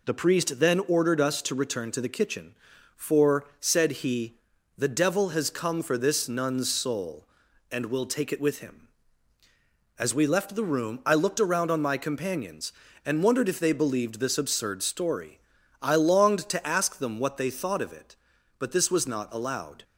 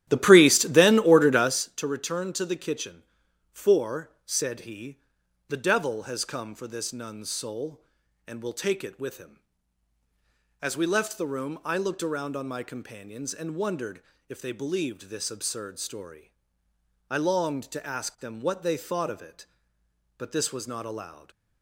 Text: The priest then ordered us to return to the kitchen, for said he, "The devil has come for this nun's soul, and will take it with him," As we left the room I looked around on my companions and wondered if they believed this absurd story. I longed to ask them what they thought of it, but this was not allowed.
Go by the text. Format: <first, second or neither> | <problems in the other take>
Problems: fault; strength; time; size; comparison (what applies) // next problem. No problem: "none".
first | starts louder than the rest; strong; until 1.7 s; 12 dB // pauses between "wondered" and "if"; slight; at 14.0 s; 0.26 s long